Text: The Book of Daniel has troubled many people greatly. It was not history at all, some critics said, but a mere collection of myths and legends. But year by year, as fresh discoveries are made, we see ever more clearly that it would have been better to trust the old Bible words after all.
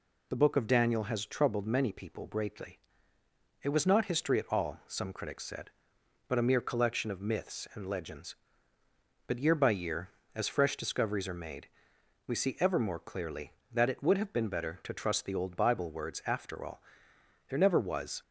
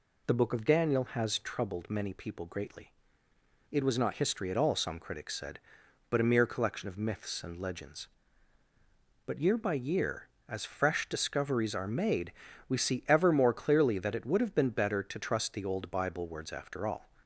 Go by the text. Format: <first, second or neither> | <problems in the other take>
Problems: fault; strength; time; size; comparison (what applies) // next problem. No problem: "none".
second | goes on to say "There never was"; noticeable; from 17.4 s on; 0.74 s long